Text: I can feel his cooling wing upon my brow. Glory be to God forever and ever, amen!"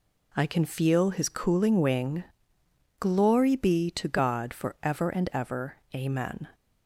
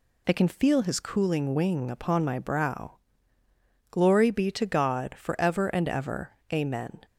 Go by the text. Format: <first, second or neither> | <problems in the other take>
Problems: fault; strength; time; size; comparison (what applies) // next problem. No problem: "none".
second | skips "upon my brow"; at 2.6 s